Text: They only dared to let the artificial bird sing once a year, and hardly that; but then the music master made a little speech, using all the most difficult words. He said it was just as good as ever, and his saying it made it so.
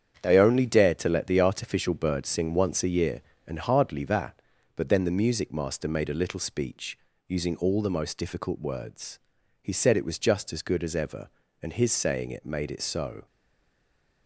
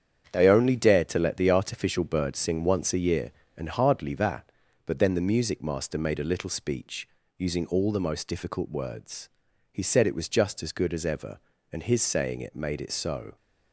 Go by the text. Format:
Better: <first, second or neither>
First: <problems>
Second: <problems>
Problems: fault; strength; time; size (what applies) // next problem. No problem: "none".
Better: second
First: starts louder than the rest; strong; until 1.2 s; 8.5 dB // stays silent after the last word; from 13.2 s on; 1.0 s long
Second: starts louder than the rest; strong; until 1.3 s; 8.5 dB